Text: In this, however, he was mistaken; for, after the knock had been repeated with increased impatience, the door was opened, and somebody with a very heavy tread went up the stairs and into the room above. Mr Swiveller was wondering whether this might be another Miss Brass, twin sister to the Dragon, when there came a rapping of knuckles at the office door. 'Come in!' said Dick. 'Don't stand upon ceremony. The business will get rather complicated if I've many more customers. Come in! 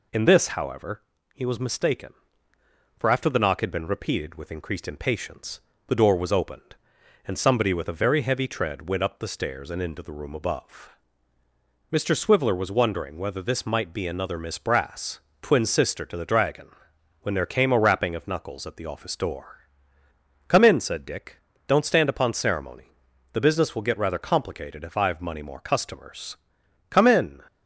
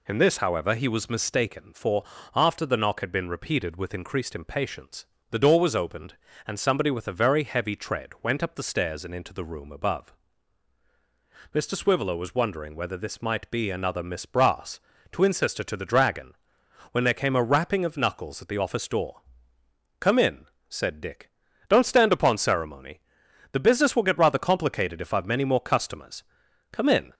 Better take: second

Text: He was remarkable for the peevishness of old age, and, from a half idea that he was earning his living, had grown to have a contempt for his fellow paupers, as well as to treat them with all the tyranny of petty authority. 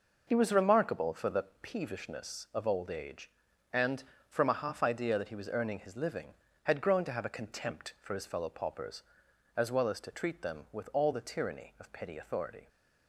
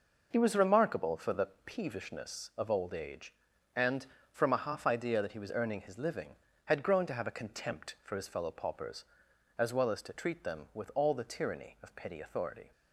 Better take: neither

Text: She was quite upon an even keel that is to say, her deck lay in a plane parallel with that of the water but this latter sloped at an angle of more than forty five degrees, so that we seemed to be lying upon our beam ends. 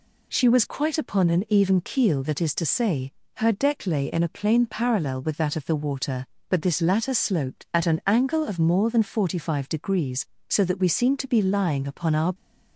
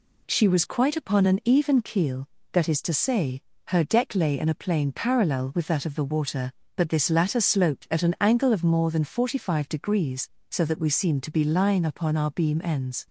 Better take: second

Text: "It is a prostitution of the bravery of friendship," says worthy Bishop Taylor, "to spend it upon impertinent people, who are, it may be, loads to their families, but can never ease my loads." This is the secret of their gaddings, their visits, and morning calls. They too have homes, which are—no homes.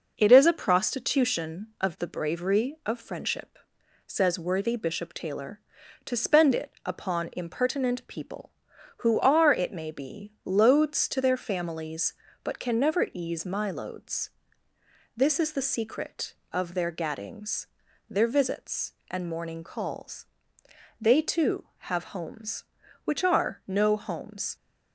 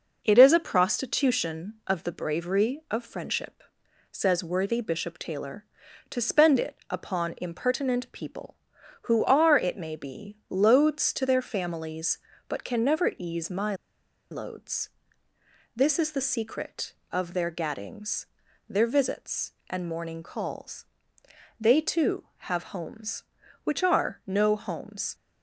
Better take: first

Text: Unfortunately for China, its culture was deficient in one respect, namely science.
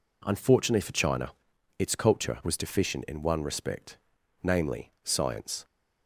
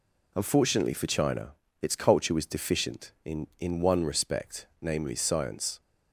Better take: first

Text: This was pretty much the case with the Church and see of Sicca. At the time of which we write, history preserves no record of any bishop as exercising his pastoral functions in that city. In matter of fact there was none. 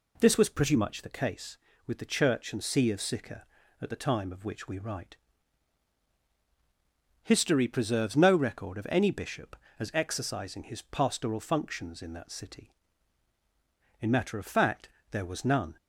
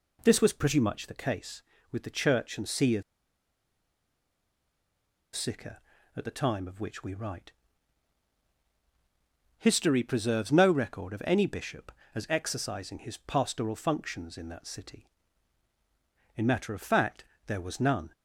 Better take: first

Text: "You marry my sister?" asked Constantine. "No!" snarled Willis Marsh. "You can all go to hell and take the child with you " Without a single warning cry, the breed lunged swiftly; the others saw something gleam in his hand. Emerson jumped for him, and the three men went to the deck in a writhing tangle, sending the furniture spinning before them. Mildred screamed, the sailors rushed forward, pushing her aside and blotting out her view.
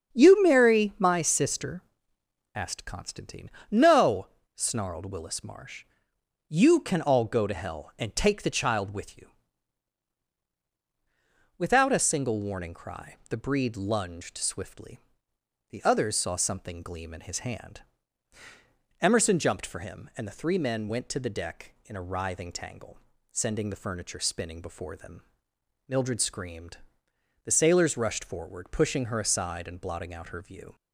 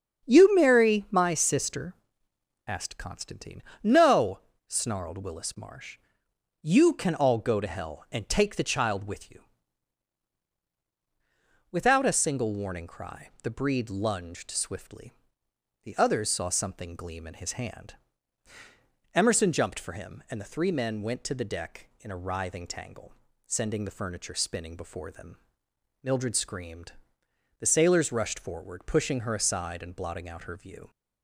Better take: neither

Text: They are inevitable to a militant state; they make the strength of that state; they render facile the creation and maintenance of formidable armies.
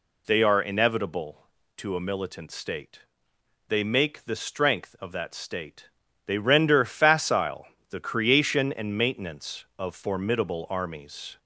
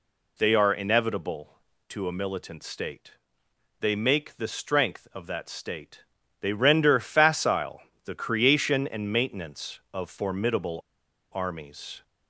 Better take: first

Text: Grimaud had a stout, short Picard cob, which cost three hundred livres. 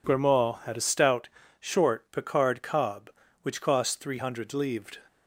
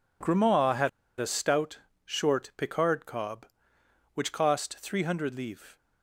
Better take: first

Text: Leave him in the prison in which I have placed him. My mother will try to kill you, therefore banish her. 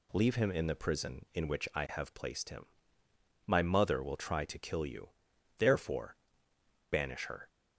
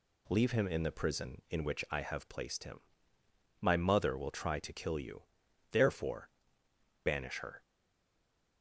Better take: first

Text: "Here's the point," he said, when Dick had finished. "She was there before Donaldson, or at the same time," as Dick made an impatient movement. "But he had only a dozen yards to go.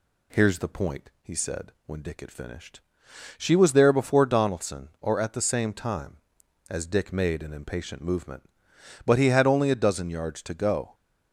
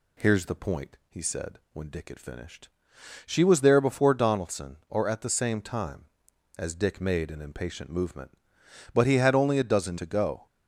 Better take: first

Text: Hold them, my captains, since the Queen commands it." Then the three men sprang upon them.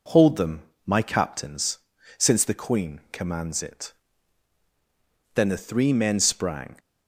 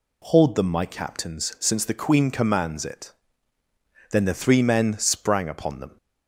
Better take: second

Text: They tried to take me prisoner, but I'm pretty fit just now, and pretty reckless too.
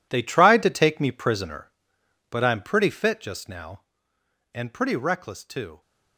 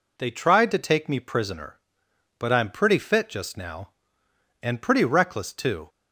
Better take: second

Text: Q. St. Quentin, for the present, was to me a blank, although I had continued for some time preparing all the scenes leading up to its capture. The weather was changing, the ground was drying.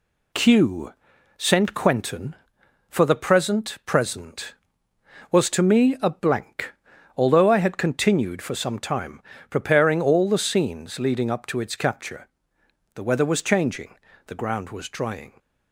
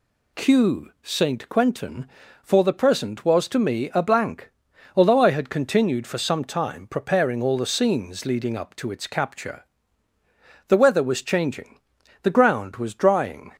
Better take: second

